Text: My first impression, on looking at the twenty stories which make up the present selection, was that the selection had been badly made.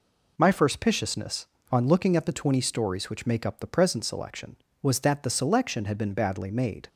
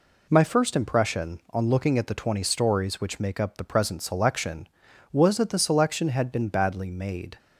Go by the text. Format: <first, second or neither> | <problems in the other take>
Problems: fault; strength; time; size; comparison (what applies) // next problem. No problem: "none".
second | says "piciousness" for "impression"; at 0.7 s